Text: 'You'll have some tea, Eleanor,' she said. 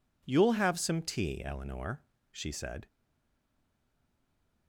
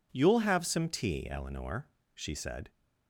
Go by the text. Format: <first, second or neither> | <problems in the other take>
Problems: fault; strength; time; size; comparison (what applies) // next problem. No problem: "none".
second | stays silent after the last word; noticeable; from 2.8 s on; 1.8 s long